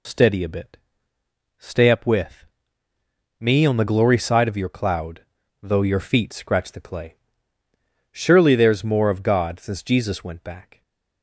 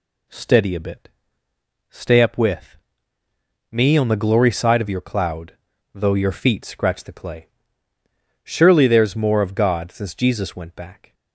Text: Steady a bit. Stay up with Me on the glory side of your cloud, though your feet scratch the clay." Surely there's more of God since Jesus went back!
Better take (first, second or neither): second